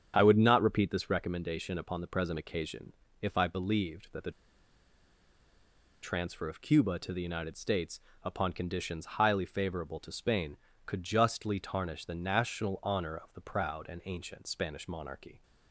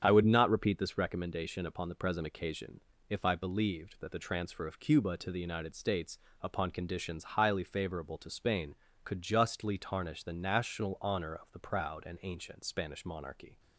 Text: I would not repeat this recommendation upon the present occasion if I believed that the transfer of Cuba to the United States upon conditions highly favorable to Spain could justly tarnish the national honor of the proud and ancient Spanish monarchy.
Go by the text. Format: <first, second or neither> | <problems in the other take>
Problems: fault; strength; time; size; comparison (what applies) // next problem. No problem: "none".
second | starts louder than the rest; strong; until 1.1 s; 8 dB; strong in the second // pauses between "occasion" and "if"; slight; at 2.9 s; 0.28 s long; slight in the second // pauses between "the" and "transfer"; strong; at 4.3 s; 1.7 s long // pauses between "States" and "upon"; slight; at 8.0 s; 0.22 s long; slight in the second